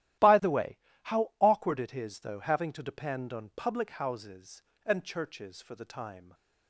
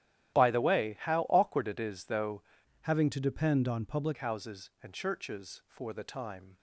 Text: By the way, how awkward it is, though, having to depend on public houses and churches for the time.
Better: first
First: starts louder than the rest; strong; until 1.6 s; 13.5 dB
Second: starts louder than the rest; strong; until 1.3 s; 12.5 dB // changes voice from "having" to "public"; from 2.8 to 4.1 s; 1.3 s long

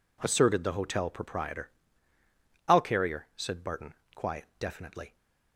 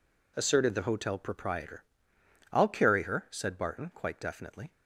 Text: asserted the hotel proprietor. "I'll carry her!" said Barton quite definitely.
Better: second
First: says "quiet" for "quite"; at 4.1 s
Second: none

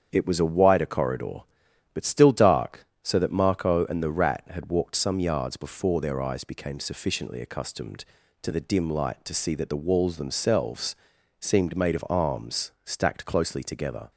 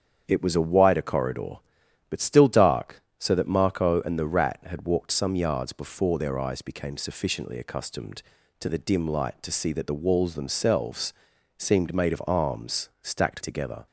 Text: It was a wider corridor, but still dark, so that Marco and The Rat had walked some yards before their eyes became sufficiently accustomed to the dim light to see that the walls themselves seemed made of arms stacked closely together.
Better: first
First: starts louder than the rest; strong; until 1.1 s; 8 dB // pauses between "themselves" and "seemed"; at 10.9 s; 0.44 s long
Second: starts louder than the rest; strong; until 1.2 s; 8 dB // pauses between "themselves" and "seemed"; at 11.1 s; 0.44 s long // skips "closely"; at 13.4 s

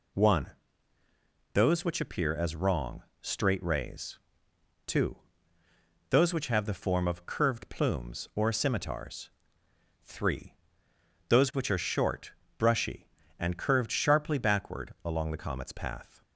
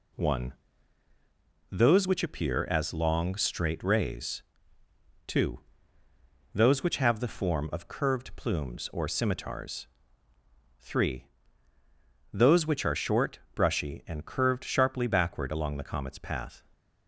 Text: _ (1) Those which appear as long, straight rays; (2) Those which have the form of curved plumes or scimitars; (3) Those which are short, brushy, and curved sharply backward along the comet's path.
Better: second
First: says "wrong" for "long"; at 2.5 s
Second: none

